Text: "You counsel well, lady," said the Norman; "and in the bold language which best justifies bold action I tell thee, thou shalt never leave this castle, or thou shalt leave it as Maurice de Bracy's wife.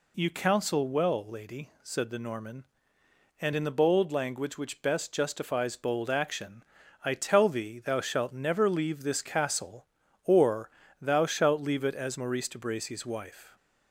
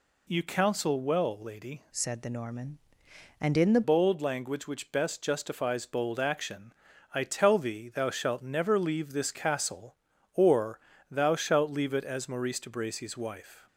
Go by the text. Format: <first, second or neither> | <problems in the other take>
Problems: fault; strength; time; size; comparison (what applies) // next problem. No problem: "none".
first | changes voice from "said" to "the"; from 1.9 to 3.8 s; 1.9 s long // pauses between "action" and "I"; at 6.7 s; 0.40 s long; also in the first // pauses between "or" and "thou"; slight; at 10.7 s; 0.32 s long; slight in the first